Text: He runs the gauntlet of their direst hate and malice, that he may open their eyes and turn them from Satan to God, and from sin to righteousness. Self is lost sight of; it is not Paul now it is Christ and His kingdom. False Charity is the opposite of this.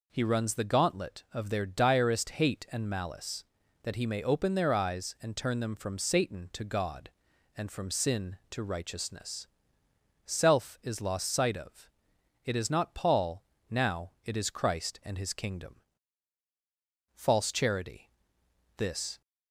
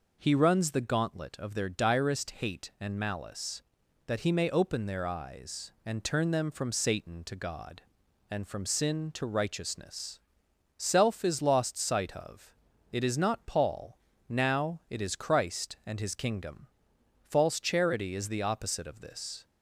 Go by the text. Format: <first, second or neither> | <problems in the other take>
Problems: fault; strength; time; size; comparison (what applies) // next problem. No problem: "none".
second | pauses between "Paul" and "now"; slight; at 13.4 s; 0.24 s long; slight in the second // skips "is the opposite of"; at 18.4 s